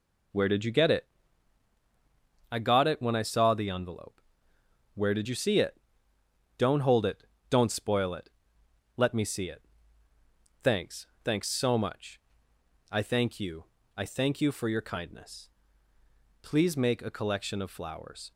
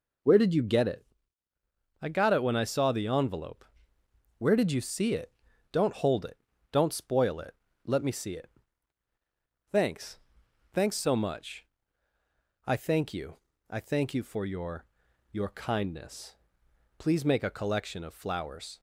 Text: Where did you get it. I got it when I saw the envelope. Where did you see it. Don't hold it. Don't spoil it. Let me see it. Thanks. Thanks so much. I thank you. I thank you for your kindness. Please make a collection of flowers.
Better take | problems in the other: first | says "your" twice; at 15.3 s

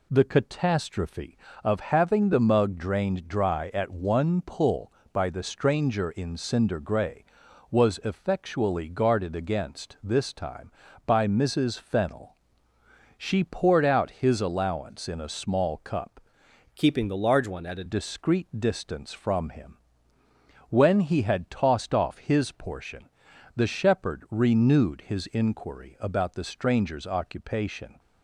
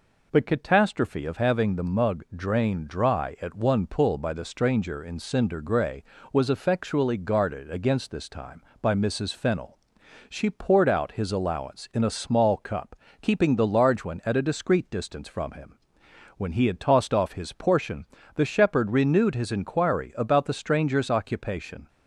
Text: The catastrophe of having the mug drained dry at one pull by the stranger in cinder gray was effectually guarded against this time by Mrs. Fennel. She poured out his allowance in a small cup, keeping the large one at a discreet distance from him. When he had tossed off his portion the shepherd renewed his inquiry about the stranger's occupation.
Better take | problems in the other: second | changes voice from "keeping" to "a"; from 16.7 to 17.8 s; 1.1 s long // pauses between "portion" and "the"; at 23.0 s; 0.44 s long; slight in the second

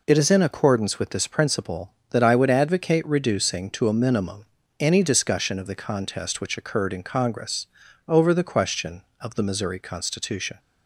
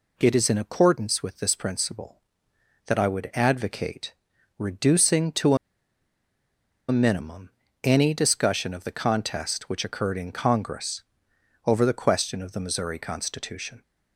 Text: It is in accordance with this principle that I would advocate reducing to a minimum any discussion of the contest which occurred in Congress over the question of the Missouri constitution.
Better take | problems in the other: first | pauses between "advocate" and "reducing"; at 4.1 s; 0.42 s long // pauses between "to" and "a"; strong; at 5.5 s; 1.3 s long // pauses between "minimum" and "any"; slight; at 7.4 s; 0.34 s long; slight in the first // pauses between "Congress" and "over"; noticeable; at 11.0 s; 0.62 s long; also in the first

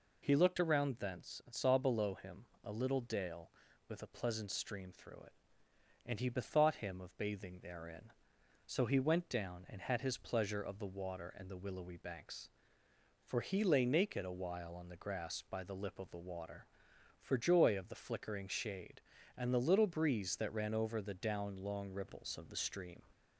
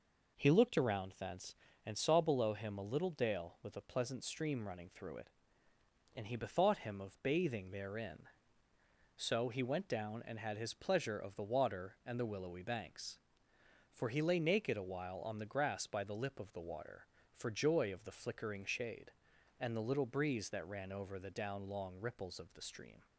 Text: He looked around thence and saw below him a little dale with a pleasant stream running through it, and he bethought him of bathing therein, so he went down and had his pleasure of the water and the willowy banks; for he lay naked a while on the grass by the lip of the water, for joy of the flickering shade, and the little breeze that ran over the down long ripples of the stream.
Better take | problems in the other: second | pauses between "him" and "a"; slight; at 2.4 s; 0.18 s long // skips "running"; at 4.8 s

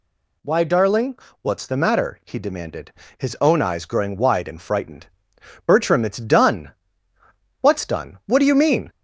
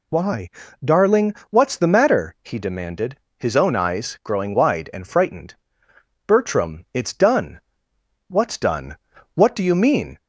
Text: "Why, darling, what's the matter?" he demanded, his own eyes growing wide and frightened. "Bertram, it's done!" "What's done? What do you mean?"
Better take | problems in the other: neither | none

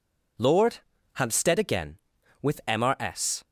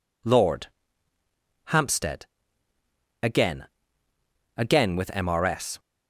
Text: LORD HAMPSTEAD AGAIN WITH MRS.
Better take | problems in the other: first | pauses between "LORD" and "HAMPSTEAD"; at 0.6 s; 1.0 s long; slight in the first // pauses between "HAMPSTEAD" and "AGAIN"; noticeable; at 2.2 s; 0.96 s long // says "AGAIN" twice; at 4.5 s

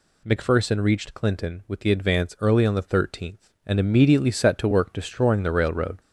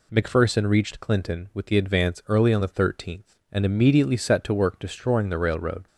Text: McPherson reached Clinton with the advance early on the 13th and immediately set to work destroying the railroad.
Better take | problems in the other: second | gets louder; noticeable; throughout; 4 dB

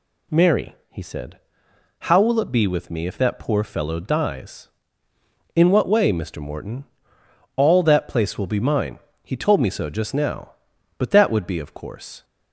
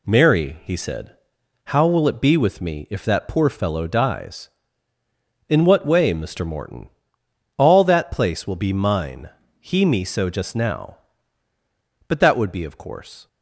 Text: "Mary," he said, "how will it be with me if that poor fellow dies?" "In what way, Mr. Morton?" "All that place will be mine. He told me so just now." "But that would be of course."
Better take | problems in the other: first | skips "told"; at 9.8 s

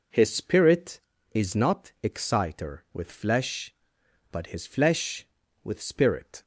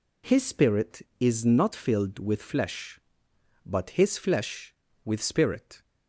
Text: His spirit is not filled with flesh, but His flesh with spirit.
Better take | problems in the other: second | says "exciter" for "filled"; at 2.0 s

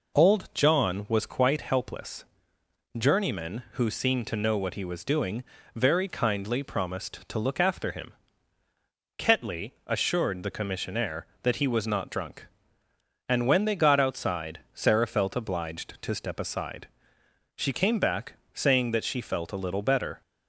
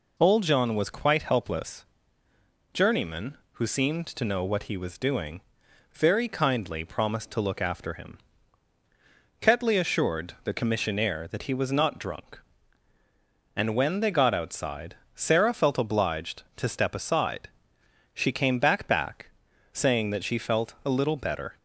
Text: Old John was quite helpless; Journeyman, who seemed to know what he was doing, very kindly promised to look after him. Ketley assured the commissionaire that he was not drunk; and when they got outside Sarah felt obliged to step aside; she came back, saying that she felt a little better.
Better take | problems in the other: first | pauses between "outside" and "Sarah"; slight; at 14.9 s; 0.18 s long; slight in the first // says "back" twice; at 18.8 s

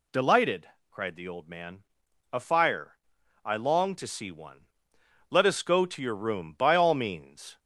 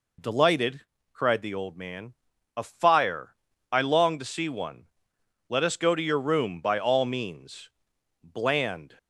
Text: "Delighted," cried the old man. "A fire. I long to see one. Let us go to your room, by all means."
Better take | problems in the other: first | goes on to say "Bland"; noticeable; from 8.2 s on; 0.76 s long

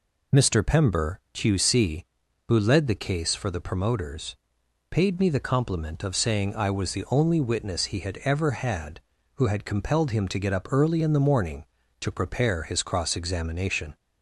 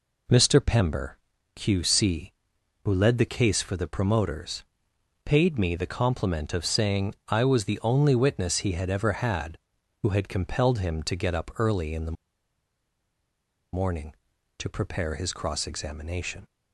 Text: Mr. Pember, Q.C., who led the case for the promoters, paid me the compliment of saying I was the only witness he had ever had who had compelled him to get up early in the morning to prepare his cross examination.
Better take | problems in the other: first | pauses between "the" and "morning"; strong; at 12.1 s; 1.6 s long

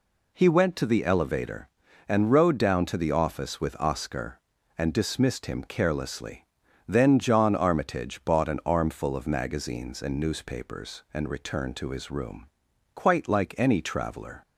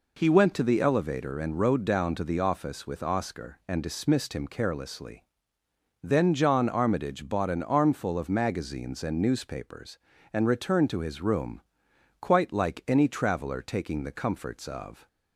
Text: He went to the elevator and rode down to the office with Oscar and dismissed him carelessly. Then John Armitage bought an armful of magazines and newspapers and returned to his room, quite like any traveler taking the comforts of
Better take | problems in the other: second | stops before "taking the comforts of"; at 14.4 s

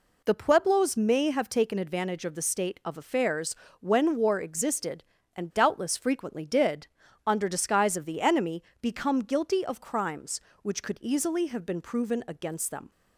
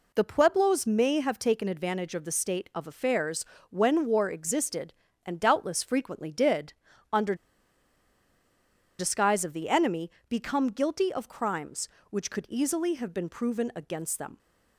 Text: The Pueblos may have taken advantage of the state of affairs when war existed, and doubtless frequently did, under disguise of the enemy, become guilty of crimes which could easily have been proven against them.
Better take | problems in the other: first | pauses between "affairs" and "when"; slight; at 3.4 s; 0.24 s long; slight in the first // pauses between "under" and "disguise"; strong; at 7.3 s; 1.6 s long

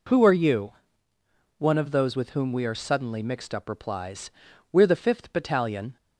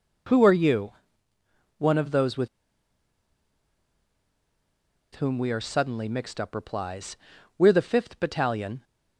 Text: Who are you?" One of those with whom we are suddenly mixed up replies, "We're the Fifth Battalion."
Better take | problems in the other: first | pauses between "with" and "whom"; strong; at 2.4 s; 2.6 s long

